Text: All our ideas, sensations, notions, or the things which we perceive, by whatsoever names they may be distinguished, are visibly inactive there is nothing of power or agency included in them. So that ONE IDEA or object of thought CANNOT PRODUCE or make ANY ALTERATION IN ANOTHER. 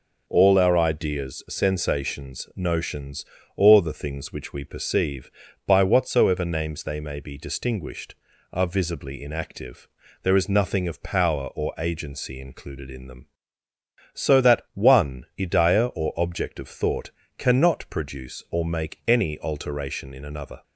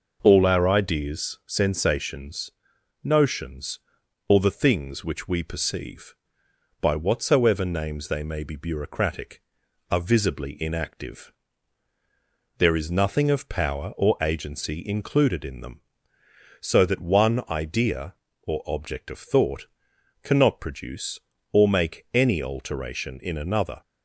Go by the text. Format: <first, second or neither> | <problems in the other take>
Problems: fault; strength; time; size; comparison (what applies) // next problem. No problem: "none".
first | says "bureaucratic" for "distinguished"; at 8.5 s // pauses between "inactive" and "there"; strong; at 11.3 s; 1.2 s long; slight in the first // pauses between "thought" and "CANNOT"; noticeable; at 19.6 s; 0.56 s long; slight in the first